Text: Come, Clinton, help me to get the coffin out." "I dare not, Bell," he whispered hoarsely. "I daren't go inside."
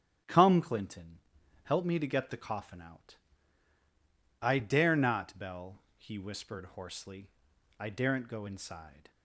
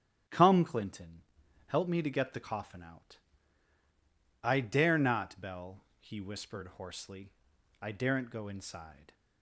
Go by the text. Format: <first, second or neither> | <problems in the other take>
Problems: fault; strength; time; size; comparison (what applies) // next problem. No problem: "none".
neither | starts louder than the rest; strong; the same in both